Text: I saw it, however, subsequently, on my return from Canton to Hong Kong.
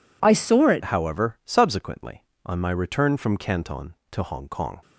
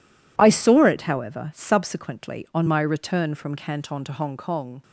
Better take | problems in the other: second | changes voice at "however"; from 0.8 s on; 3.9 s long

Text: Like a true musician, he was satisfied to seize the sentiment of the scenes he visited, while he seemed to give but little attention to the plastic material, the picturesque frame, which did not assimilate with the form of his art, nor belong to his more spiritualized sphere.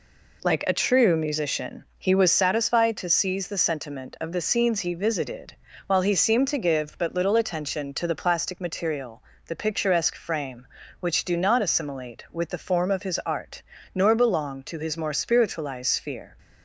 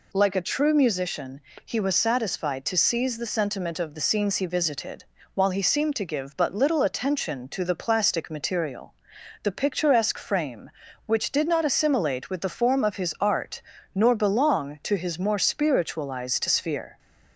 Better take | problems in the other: second | says "do" for "did"; at 11.2 s

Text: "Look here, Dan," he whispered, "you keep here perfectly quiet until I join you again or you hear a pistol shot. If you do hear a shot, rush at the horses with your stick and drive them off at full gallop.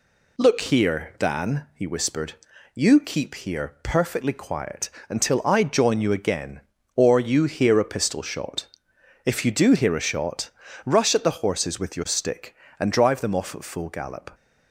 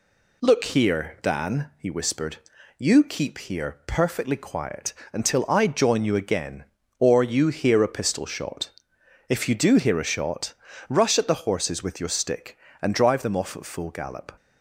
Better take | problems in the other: neither | pauses between "quiet" and "until"; slight; the same in both

